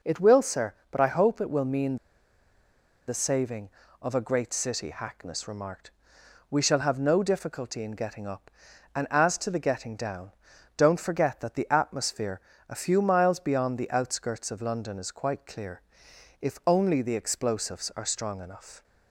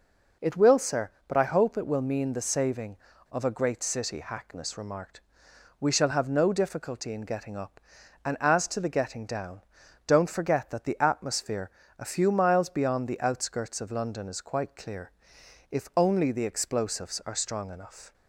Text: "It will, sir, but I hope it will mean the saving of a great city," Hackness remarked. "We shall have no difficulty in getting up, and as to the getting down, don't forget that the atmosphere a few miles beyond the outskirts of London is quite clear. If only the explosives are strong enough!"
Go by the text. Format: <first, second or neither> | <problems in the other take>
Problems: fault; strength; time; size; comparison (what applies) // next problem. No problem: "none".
second | pauses between "mean" and "the"; at 1.9 s; 1.0 s long // pauses between "atmosphere" and "a"; slight; at 12.4 s; 0.28 s long; slight in the second